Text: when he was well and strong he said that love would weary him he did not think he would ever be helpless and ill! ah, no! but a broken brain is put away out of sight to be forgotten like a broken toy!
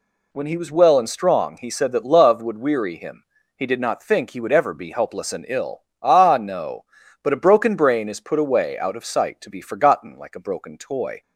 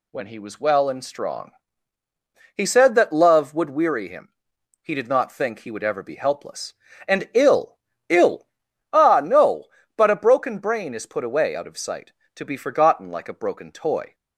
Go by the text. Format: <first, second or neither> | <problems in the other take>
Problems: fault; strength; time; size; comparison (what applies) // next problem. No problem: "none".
first | pauses between "strong" and "he"; at 1.5 s; 1.0 s long // pauses between "him" and "he"; noticeable; at 4.2 s; 0.54 s long; slight in the first // says "ill" twice; at 8.0 s